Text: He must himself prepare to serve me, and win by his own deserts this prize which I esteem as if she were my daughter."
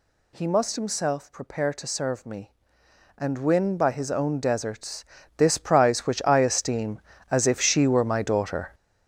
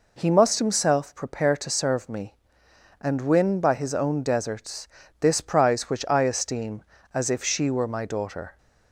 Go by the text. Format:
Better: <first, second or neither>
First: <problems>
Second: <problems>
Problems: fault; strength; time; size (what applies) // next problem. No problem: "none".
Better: second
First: gets louder; strong; throughout; 9 dB // pauses between "deserts" and "this"; slight; at 5.0 s; 0.32 s long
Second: pauses between "deserts" and "this"; slight; at 4.8 s; 0.32 s long